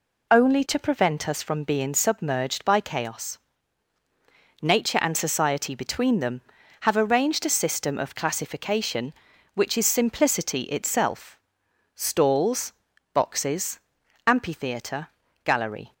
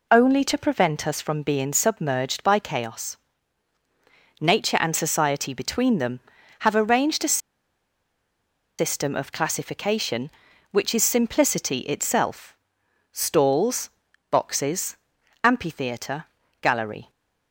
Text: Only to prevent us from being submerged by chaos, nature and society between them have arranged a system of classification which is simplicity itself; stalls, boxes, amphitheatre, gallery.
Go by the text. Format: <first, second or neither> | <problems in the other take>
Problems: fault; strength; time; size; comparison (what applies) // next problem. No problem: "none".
first | pauses between "a" and "system"; strong; at 7.3 s; 1.4 s long